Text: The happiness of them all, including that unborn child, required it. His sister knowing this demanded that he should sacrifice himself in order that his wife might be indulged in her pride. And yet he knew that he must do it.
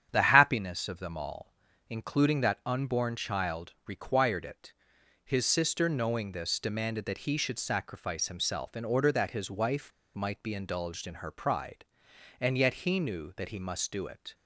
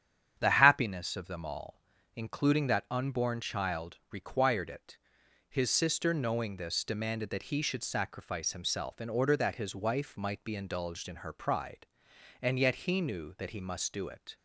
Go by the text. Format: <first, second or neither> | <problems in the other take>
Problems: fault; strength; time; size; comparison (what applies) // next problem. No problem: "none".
second | starts louder than the rest; strong; until 1.1 s; 9 dB; strong in the second // pauses between "wife" and "might"; slight; at 9.9 s; 0.25 s long